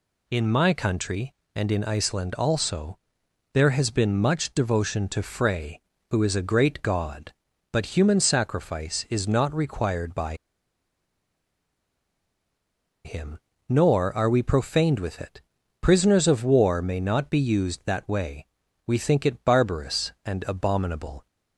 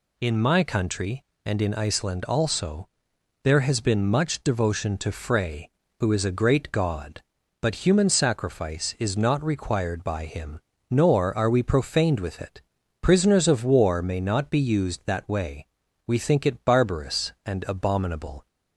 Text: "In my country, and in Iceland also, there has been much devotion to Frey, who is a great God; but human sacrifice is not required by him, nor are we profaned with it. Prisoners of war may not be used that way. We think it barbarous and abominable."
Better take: second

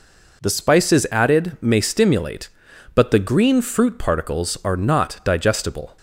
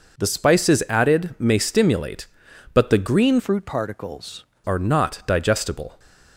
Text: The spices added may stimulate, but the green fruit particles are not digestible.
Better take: first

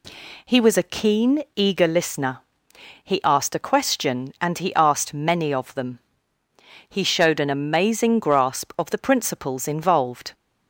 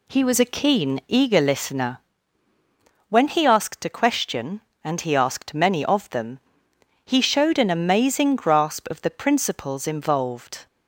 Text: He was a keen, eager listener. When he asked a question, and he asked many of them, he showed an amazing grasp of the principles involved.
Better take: second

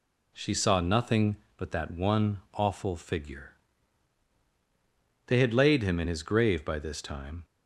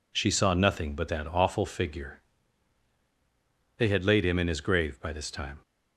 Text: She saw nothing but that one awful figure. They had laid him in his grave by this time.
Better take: first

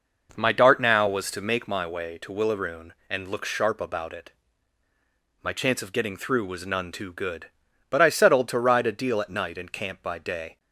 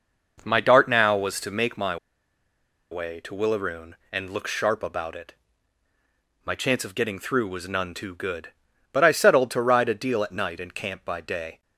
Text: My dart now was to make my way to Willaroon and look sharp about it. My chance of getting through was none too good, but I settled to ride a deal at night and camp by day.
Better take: first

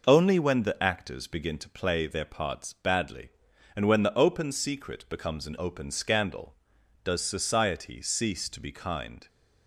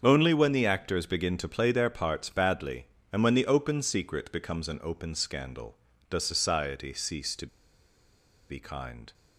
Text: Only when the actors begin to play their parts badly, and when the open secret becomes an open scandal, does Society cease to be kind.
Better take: first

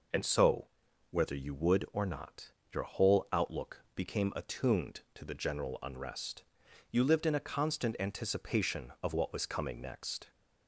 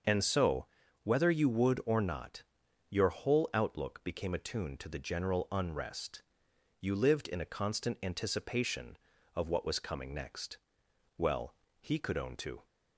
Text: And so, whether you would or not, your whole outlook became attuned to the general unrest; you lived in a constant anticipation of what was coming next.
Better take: first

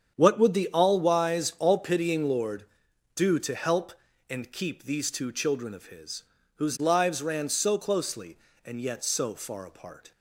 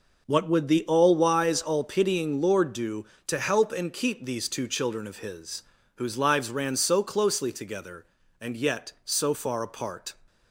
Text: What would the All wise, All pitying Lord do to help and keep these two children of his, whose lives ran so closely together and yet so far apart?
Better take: second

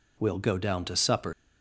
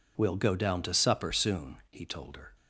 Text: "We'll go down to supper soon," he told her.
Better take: second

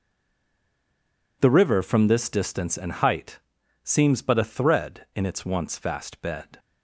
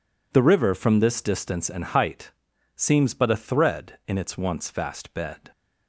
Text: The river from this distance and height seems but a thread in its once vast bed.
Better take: second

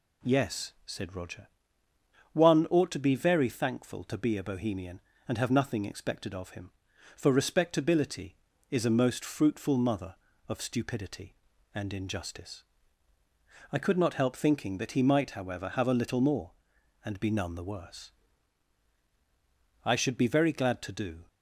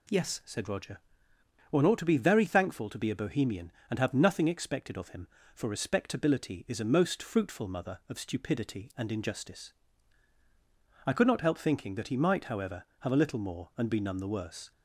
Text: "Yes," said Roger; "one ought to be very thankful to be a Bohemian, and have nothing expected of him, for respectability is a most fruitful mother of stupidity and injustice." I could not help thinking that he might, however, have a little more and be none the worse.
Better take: second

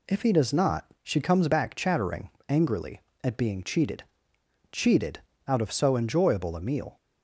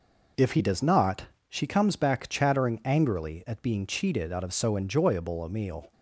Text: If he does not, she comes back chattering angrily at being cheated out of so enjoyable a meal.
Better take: second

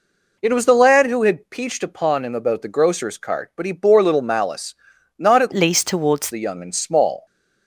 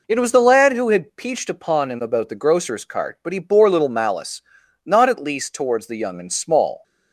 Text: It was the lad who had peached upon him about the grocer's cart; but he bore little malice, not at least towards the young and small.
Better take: second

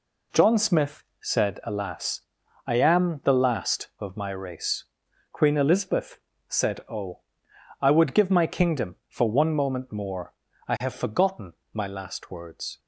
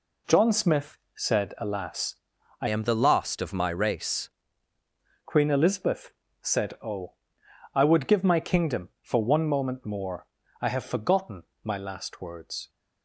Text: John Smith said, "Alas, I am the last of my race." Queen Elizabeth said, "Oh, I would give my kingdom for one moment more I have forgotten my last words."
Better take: first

